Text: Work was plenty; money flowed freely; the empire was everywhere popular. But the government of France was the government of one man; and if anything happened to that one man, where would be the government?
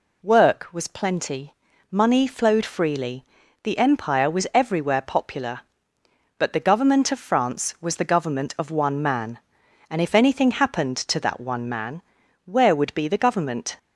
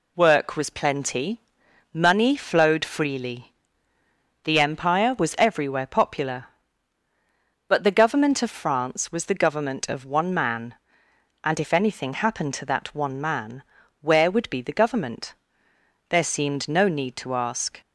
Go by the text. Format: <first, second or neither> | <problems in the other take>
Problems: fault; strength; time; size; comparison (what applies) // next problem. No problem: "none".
first | goes on to say "There seemed no need to ask"; strong; from 16.0 s on; 1.7 s long